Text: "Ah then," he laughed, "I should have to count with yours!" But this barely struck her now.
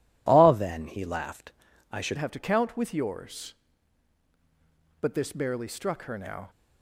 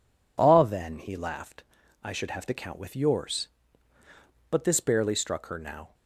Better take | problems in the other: second | changes voice at "have"; from 2.1 s on; 4.3 s long

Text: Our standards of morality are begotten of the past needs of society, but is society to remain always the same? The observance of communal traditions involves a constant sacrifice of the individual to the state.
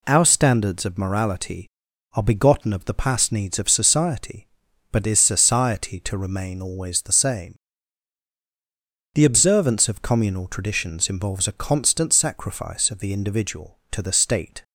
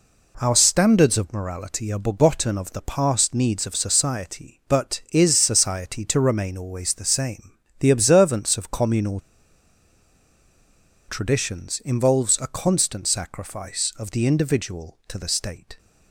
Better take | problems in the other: first | pauses between "communal" and "traditions"; strong; at 9.1 s; 1.8 s long

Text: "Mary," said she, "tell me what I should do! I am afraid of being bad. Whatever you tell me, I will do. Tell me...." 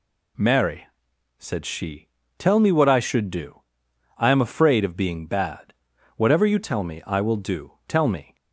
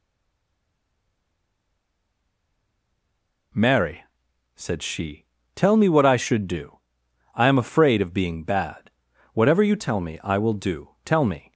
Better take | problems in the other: first | stays silent before the first word; strong; until 3.5 s; 3.5 s long

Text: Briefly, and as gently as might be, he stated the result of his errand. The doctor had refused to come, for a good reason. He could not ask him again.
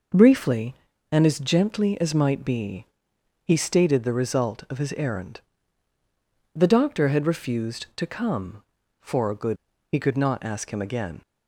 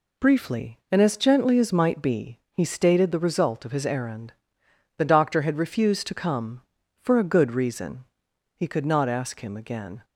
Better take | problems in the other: second | skips "reason"; at 9.7 s

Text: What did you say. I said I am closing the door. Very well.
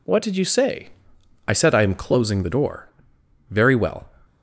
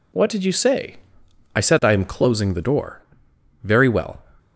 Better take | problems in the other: neither | none

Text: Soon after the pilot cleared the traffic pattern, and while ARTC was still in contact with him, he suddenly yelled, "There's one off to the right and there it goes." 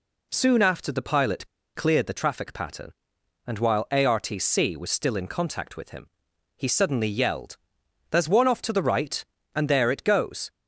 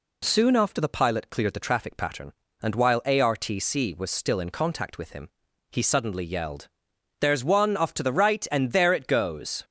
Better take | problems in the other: second | pauses between "pilot" and "cleared"; slight; at 1.4 s; 0.28 s long

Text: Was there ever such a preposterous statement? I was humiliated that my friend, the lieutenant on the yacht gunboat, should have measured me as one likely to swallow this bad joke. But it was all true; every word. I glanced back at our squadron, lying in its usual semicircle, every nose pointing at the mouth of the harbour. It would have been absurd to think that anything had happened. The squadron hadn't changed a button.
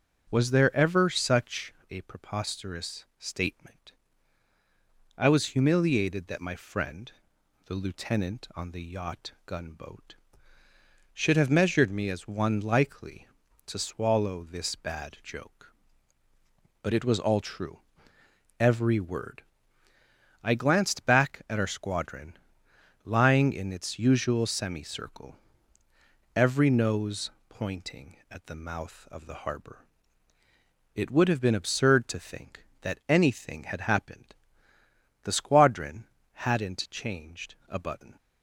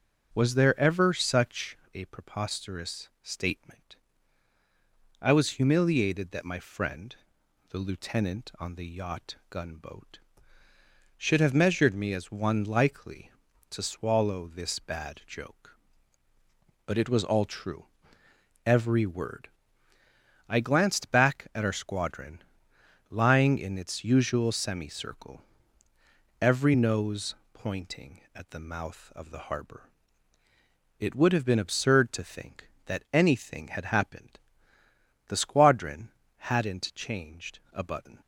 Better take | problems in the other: neither | starts louder than the rest; noticeable; the same in both // pauses between "such" and "a"; slight; the same in both // pauses between "yacht" and "gunboat"; slight; the same in both // pauses between "nose" and "pointing"; slight; the same in both // pauses between "squadron" and "hadn't"; slight; the same in both

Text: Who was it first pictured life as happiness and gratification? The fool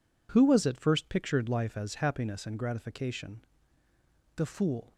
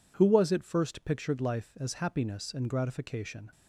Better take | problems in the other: first | stops before "The fool"; at 3.5 s

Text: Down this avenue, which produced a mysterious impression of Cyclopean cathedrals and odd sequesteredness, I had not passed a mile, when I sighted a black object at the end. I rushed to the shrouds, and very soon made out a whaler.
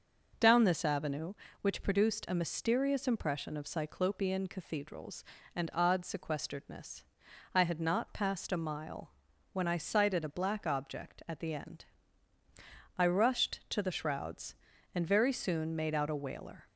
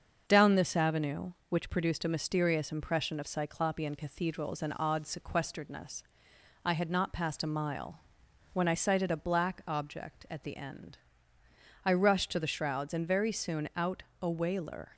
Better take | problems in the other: first | starts louder than the rest; until 1.2 s; 6.5 dB // skips "made"; at 13.7 s // pauses between "out" and "a"; slight; at 14.0 s; 0.20 s long

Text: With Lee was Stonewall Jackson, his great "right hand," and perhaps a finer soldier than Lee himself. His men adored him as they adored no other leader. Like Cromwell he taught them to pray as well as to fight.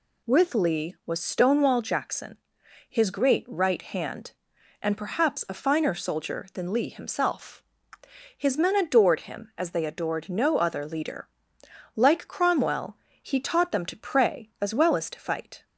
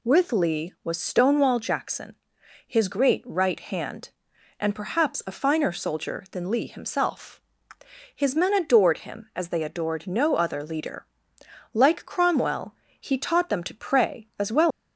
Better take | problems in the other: first | pauses between "Cromwell" and "he"; slight; at 12.7 s; 0.24 s long; slight in the first // stops before "as to fight"; at 14.7 s

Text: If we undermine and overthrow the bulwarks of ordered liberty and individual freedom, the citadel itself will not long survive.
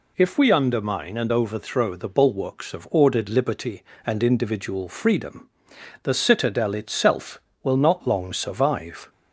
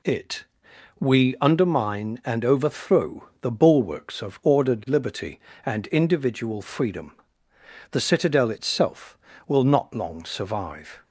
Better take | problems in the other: first | says "It" for "If"; at 0.0 s

